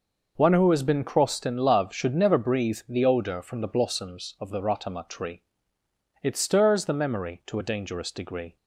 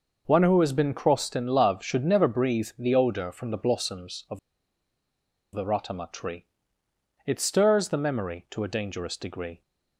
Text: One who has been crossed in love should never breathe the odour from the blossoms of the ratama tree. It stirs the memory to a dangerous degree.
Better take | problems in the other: first | pauses between "of" and "the"; at 4.3 s; 1.1 s long

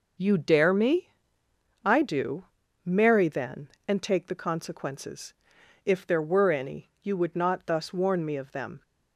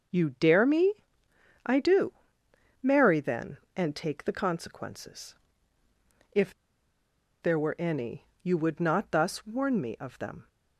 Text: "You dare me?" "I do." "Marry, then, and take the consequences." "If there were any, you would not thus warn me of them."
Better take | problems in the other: first | starts louder than the rest; noticeable; until 1.7 s; 6 dB // pauses between "If" and "there"; noticeable; at 6.5 s; 0.91 s long

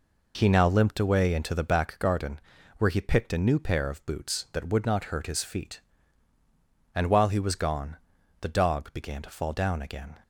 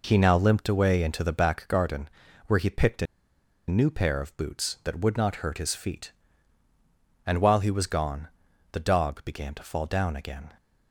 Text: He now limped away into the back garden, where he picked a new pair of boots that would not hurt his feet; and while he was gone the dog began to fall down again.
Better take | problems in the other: first | pauses between "a" and "new"; noticeable; at 3.0 s; 0.63 s long // pauses between "gone" and "the"; noticeable; at 8.2 s; 0.46 s long; noticeable in the first

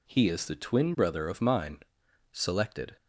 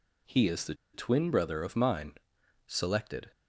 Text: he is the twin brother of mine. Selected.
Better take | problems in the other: first | pauses between "the" and "twin"; slight; at 0.7 s; 0.19 s long

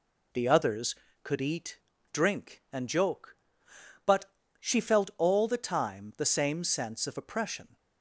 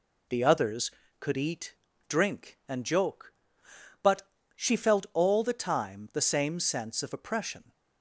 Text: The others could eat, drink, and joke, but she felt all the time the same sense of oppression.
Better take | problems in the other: neither | pauses between "but" and "she"; slight; the same in both

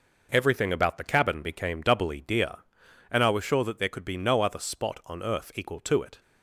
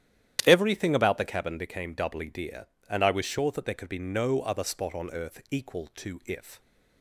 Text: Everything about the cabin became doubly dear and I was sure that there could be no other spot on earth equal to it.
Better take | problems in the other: first | starts louder than the rest; strong; until 1.4 s; 11 dB // says "if" for "it"; at 6.2 s

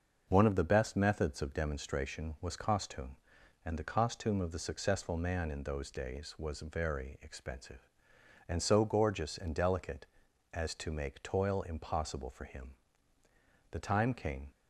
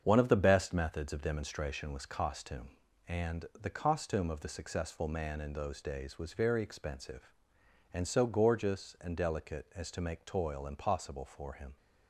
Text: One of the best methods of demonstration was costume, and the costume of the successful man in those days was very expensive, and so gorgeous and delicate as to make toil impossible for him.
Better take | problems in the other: second | starts louder than the rest; until 1.2 s; 6.5 dB; strong in the second // goes on to say "The time came"; noticeable; from 13.7 s on; 0.80 s long

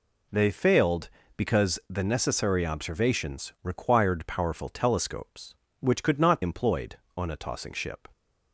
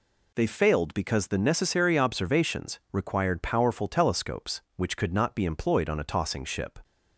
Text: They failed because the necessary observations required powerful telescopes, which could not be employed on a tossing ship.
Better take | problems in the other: second | skips "be"; at 6.4 s

